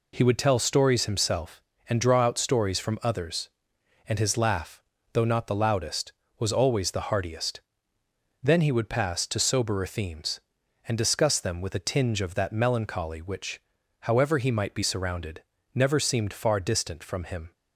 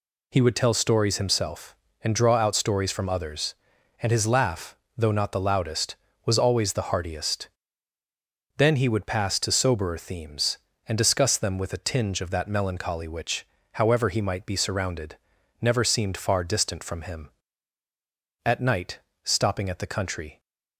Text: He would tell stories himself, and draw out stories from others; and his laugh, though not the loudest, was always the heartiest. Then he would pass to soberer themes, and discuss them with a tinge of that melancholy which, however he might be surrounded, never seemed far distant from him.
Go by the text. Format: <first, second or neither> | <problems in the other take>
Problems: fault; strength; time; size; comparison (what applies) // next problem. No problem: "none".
first | goes on to say "At night stopping at the country"; strong; from 18.4 s on; 1.9 s long